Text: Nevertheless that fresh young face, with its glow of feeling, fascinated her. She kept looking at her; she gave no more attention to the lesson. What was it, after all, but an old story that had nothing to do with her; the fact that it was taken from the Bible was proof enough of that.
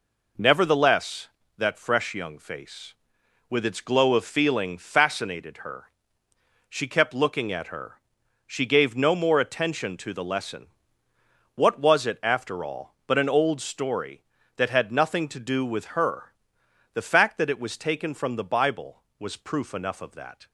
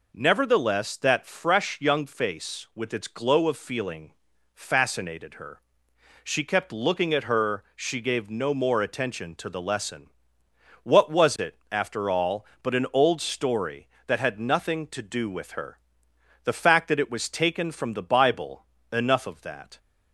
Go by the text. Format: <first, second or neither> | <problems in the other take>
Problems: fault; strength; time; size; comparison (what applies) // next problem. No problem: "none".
first | skips "was proof"; at 18.7 s